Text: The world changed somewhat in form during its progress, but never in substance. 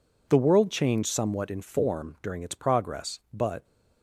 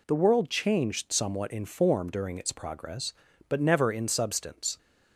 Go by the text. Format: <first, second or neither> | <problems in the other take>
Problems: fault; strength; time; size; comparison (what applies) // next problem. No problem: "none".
second | stops before "never in substance"; at 3.6 s